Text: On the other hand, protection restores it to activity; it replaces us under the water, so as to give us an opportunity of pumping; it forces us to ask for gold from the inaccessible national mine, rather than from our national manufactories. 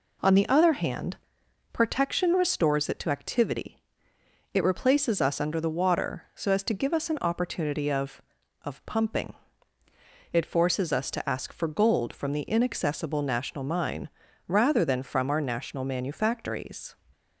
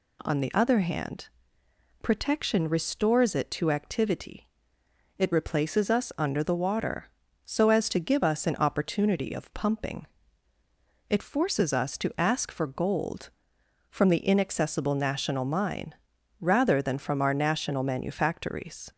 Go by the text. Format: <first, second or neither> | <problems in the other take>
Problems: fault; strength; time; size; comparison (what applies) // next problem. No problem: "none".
second | says "of" twice; at 8.6 s